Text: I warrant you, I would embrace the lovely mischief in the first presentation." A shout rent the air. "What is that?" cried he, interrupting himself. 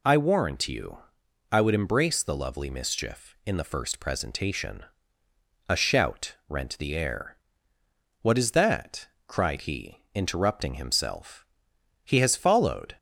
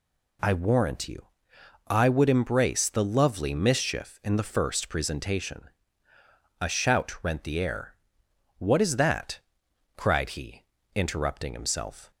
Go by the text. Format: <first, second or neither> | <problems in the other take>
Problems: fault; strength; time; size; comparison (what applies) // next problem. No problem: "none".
second | goes on to say "He has followed"; noticeable; from 12.0 s on; 0.90 s long